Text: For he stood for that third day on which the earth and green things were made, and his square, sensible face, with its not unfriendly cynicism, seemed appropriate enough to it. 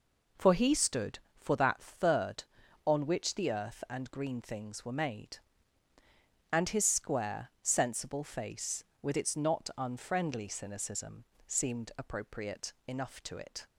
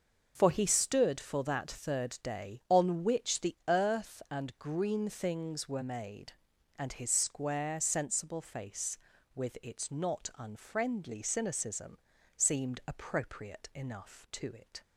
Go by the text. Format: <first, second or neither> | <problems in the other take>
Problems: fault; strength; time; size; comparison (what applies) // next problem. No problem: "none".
second | skips "day"; at 2.6 s // pauses between "appropriate" and "enough"; slight; at 12.7 s; 0.16 s long